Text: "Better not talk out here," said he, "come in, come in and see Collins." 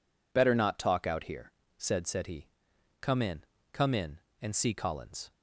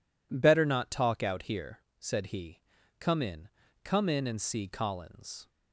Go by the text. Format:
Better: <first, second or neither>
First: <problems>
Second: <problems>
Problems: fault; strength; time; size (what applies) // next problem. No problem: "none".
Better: second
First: says "said" twice; at 2.0 s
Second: none